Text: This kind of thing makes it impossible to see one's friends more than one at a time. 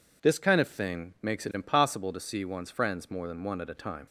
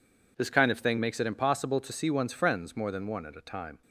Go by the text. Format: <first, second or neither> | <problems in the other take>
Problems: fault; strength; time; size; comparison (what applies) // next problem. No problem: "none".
neither | none